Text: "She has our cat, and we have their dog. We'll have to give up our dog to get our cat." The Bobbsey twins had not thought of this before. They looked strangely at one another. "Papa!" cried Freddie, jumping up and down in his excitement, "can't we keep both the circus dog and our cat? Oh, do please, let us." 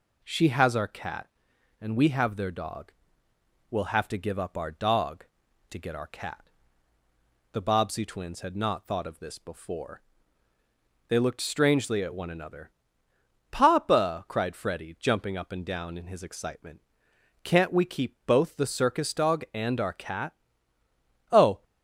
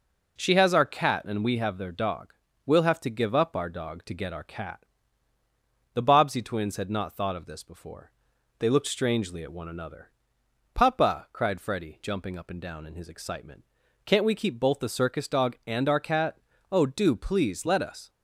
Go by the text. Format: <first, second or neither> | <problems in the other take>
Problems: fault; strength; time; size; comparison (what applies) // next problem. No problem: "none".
second | stops before "do please let us"; at 21.6 s